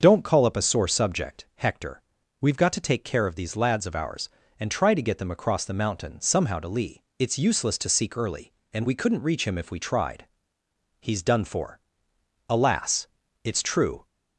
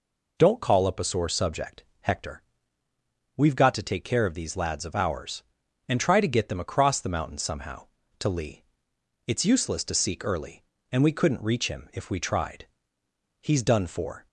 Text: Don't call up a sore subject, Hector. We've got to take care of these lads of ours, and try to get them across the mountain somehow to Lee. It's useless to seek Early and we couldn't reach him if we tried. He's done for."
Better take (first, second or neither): second